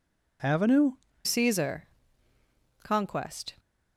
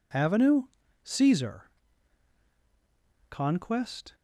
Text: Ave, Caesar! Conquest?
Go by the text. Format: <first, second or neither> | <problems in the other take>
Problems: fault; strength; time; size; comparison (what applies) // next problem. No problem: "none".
second | changes voice at "Caesar"; from 1.2 s on; 2.3 s long